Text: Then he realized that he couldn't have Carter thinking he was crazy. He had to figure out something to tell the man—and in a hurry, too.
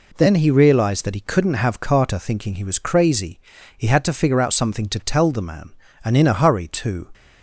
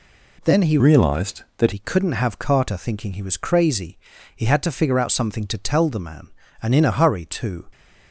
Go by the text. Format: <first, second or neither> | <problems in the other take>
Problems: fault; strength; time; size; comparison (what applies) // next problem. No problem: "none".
first | changes voice from "realized" to "that"; from 0.7 to 1.7 s; 1.0 s long